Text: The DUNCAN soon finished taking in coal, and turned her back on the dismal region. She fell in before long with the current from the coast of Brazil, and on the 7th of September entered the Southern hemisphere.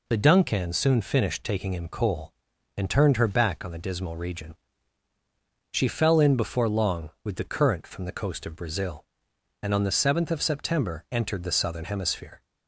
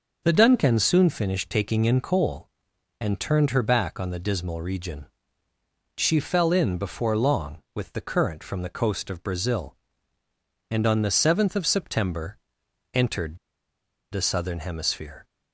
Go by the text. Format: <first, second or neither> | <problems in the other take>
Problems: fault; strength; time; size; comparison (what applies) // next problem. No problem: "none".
first | pauses between "September" and "entered"; noticeable; at 12.3 s; 0.56 s long // pauses between "entered" and "the"; noticeable; at 13.3 s; 0.75 s long